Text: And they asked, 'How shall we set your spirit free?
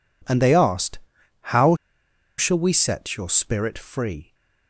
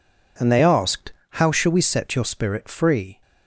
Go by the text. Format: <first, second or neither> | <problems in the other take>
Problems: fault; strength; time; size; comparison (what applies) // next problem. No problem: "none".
second | pauses between "How" and "shall"; noticeable; at 1.7 s; 0.63 s long